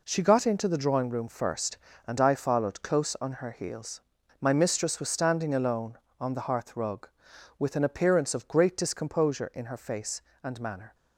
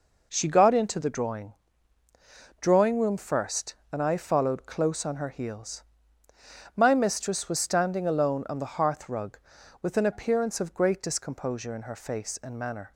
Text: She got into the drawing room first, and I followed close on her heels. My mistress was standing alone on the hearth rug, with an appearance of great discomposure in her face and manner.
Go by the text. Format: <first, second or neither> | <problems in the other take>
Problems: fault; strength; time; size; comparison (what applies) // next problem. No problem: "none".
first | says "drawing" twice; at 2.5 s